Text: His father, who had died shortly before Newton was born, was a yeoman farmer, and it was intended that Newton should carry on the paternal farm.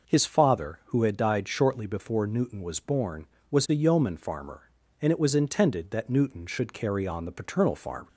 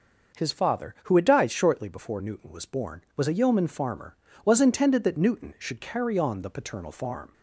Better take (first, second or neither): first